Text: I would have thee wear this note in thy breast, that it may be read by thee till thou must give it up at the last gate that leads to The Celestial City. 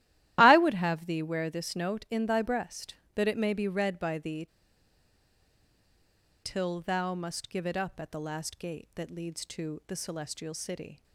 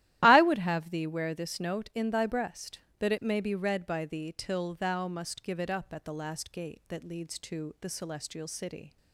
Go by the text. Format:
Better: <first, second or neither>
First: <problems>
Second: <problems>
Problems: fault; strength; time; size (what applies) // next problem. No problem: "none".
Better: second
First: starts louder than the rest; strong; until 1.4 s; 14 dB // pauses between "thee" and "till"; strong; at 4.4 s; 1.9 s long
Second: starts louder than the rest; strong; until 1.2 s; 14 dB